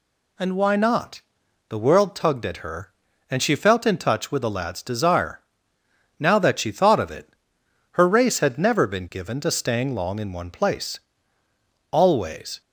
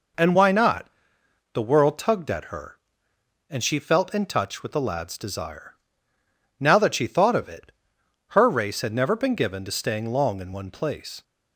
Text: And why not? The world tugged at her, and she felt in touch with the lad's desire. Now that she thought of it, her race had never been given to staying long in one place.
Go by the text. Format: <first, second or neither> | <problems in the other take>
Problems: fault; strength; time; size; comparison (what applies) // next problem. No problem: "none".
second | goes on to say "Always"; noticeable; from 11.9 s on; 0.70 s long